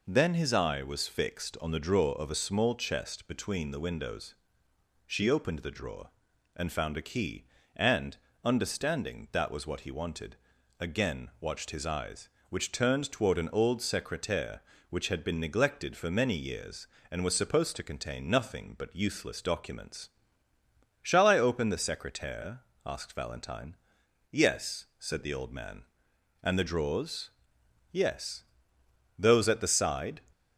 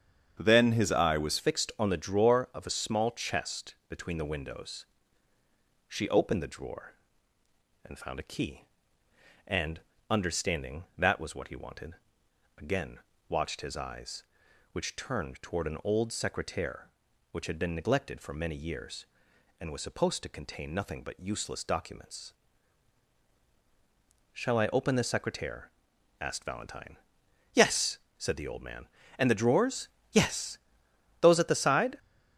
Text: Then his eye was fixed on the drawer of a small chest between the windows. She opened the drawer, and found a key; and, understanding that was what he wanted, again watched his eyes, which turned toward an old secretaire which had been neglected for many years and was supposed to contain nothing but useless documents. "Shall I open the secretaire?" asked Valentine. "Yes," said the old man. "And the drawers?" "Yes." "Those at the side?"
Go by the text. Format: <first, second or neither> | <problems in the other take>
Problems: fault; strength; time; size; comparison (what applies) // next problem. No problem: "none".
first | starts louder than the rest; strong; until 1.4 s; 8 dB // changes voice at "fixed"; from 1.3 s on; 30.6 s long // pauses between "again" and "watched"; slight; at 12.9 s; 0.30 s long